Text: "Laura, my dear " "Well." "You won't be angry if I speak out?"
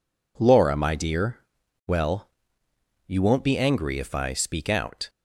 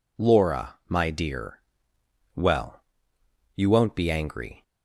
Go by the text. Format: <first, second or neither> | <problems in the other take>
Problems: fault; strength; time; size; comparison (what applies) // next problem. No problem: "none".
first | stops before "if I speak out"; at 4.6 s